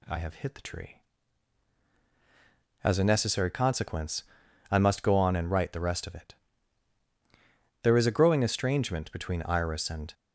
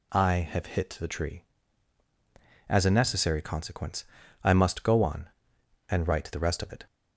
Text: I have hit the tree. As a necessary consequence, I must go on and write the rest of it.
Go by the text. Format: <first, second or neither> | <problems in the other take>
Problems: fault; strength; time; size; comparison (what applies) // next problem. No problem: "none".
second | goes on to say "There is a growing estrangement between Iris and"; strong; from 7.8 s on; 2.3 s long